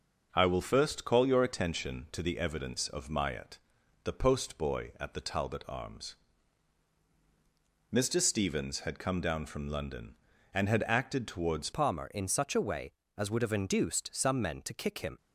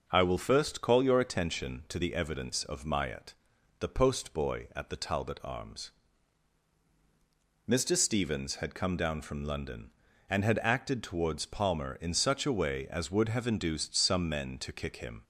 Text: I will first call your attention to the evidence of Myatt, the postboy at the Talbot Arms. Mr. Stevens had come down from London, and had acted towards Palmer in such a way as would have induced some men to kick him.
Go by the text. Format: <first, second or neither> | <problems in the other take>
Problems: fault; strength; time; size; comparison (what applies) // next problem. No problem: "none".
second | changes voice at "Palmer"; from 11.7 s on; 3.4 s long